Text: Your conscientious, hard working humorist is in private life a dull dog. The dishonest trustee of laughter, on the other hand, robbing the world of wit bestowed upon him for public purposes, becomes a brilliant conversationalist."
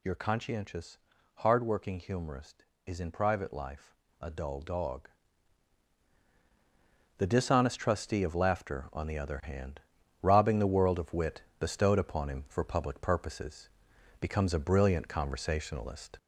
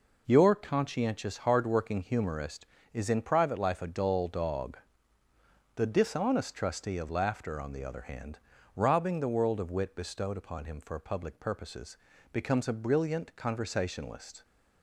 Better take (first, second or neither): second